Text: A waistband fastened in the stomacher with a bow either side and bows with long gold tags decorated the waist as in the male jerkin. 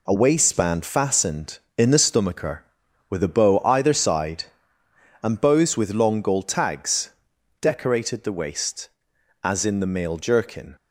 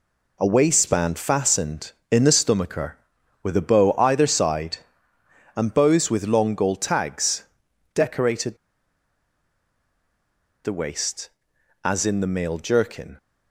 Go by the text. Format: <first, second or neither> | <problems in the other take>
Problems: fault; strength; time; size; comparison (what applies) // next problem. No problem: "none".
first | pauses between "tags" and "decorated"; noticeable; at 7.4 s; 0.52 s long; noticeable in the first // pauses between "decorated" and "the"; strong; at 8.5 s; 2.0 s long